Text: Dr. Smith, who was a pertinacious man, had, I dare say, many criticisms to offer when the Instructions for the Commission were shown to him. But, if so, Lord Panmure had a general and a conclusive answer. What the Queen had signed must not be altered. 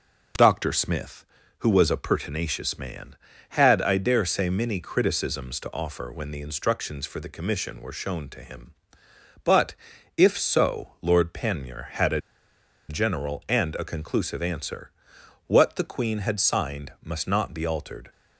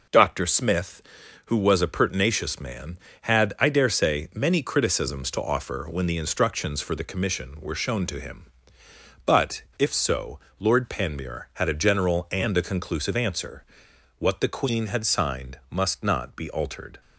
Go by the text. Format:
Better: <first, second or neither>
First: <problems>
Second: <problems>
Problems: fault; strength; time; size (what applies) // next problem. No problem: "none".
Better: second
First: pauses between "a" and "general"; noticeable; at 12.2 s; 0.68 s long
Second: none